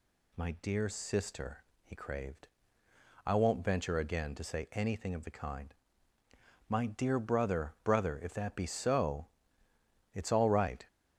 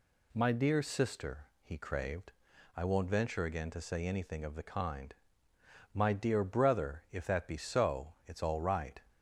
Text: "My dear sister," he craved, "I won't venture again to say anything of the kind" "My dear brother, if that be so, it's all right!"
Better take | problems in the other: second | pauses between "kind" and "My"; noticeable; at 5.7 s; 0.94 s long; noticeable in the second // says "brother" twice; at 7.8 s

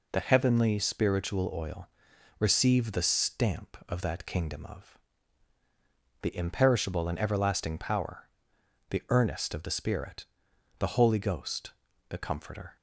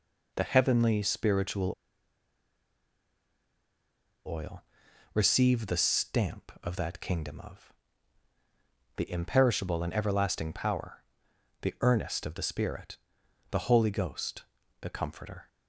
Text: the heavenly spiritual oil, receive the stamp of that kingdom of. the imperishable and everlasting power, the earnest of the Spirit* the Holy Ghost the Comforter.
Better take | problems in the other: first | pauses between "spiritual" and "oil"; strong; at 1.7 s; 2.5 s long // pauses between "Spirit" and "the"; noticeable; at 12.9 s; 0.54 s long; noticeable in the first // pauses between "Ghost" and "the"; at 14.4 s; 0.38 s long; also in the first

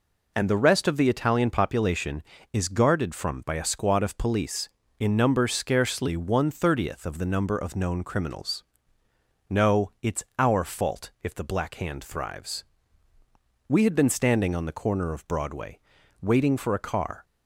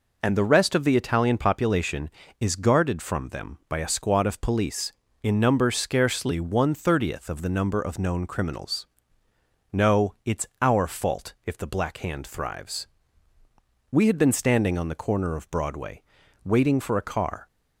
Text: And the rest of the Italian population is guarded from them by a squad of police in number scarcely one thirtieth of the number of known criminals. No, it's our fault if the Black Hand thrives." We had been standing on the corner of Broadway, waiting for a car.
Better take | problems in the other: second | skips "them"; at 3.4 s

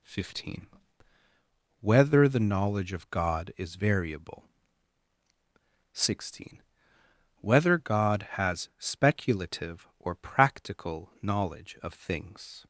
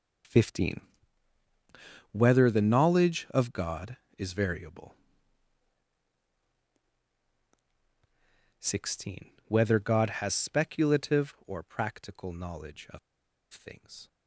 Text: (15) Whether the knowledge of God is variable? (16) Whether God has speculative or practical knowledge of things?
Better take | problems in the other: first | pauses between "of" and "things"; noticeable; at 12.9 s; 0.54 s long

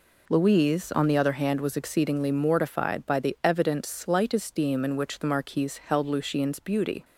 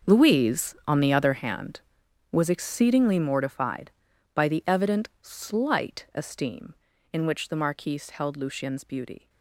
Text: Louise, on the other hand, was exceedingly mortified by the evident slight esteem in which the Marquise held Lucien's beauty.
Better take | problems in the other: first | gets quieter; strong; throughout; 15 dB

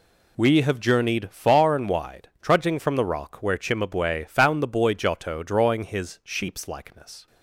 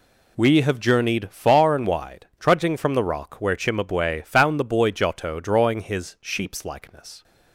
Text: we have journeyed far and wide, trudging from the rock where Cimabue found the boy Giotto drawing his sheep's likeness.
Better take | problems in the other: neither | none

